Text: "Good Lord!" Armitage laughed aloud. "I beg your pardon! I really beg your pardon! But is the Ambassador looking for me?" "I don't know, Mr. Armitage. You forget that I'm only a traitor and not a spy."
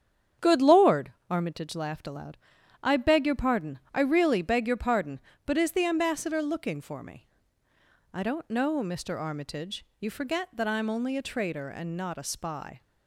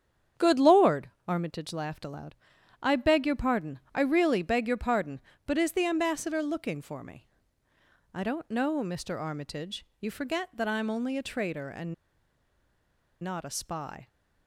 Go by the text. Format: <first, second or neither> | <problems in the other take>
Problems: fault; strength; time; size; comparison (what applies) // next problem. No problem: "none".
first | starts louder than the rest; strong; until 1.5 s; 8.5 dB; strong in the first // pauses between "and" and "not"; strong; at 11.9 s; 1.2 s long